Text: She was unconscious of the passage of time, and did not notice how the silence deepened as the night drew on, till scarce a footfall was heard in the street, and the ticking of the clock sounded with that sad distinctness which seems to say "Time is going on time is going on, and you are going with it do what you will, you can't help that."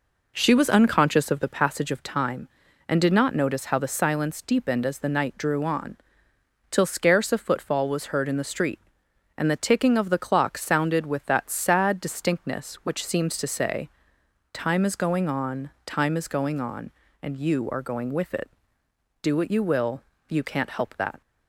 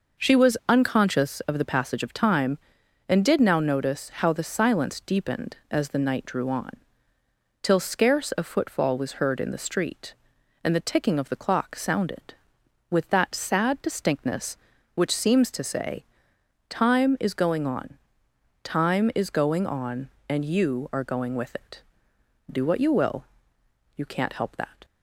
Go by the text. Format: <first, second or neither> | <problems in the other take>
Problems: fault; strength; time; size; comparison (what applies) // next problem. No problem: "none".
first | says "now" for "not"; at 3.3 s // pauses between "say" and "Time"; noticeable; at 16.0 s; 0.66 s long; noticeable in the first // pauses between "on" and "time"; noticeable; at 17.9 s; 0.68 s long